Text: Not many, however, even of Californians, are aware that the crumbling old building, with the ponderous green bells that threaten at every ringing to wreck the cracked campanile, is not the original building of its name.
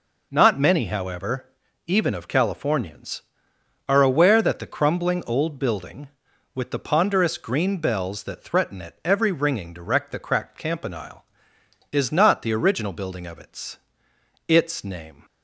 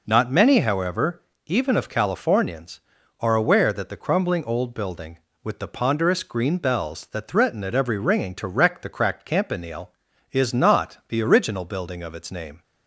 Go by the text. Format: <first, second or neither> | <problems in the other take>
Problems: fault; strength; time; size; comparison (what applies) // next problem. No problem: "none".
second | says "its" twice; at 14.4 s